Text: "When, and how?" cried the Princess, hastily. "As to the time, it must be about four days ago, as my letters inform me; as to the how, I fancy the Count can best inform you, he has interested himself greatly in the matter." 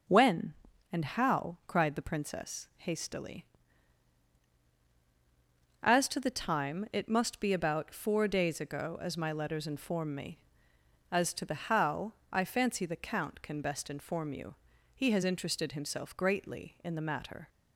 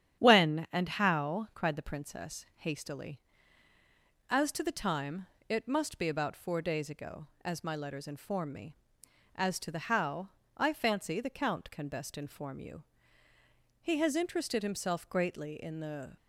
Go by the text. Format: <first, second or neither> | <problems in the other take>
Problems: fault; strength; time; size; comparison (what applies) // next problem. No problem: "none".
first | starts louder than the rest; strong; until 1.2 s; 10 dB // stops before "matter"; at 16.1 s